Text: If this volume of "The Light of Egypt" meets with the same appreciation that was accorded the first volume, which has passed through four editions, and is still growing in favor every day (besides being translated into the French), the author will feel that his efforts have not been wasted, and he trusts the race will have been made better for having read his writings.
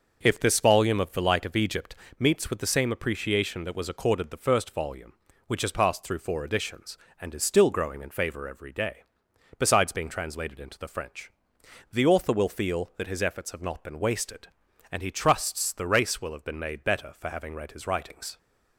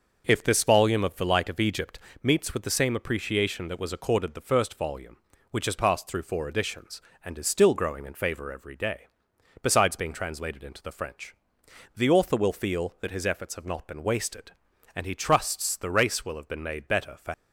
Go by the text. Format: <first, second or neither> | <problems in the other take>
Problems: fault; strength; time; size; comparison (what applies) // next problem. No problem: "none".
first | starts louder than the rest; noticeable; until 1.2 s; 6 dB; noticeable in the first // pauses between "Egypt" and "meets"; slight; at 1.9 s; 0.24 s long; slight in the first // stops before "having read his writings"; at 17.3 s